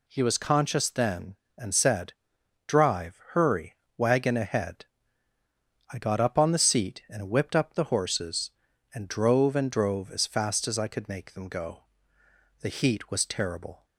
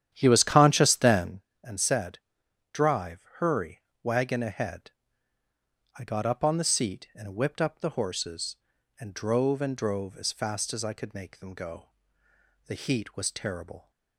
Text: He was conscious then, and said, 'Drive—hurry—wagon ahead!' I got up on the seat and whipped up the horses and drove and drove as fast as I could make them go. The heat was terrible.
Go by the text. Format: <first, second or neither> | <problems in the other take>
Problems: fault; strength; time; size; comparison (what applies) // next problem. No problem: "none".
first | starts louder than the rest; strong; until 1.5 s; 10 dB